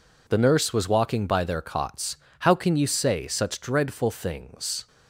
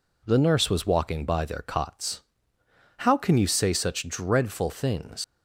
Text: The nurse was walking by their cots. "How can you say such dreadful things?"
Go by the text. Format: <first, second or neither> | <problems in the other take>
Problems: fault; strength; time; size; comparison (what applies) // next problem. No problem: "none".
first | leaves "things" unfinished; at 5.2 s; 105 ms